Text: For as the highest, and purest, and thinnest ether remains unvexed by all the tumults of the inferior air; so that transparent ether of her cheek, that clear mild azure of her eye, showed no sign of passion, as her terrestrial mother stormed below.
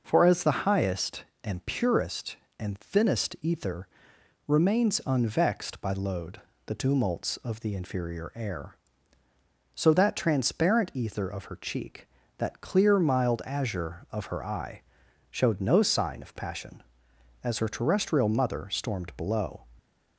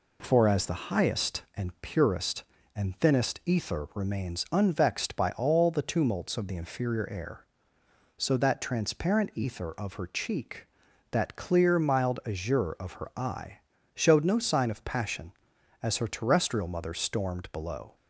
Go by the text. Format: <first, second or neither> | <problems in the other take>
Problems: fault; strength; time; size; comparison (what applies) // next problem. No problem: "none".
second | pauses between "ether" and "remains"; noticeable; at 3.8 s; 0.58 s long // says "load" for "all"; at 5.9 s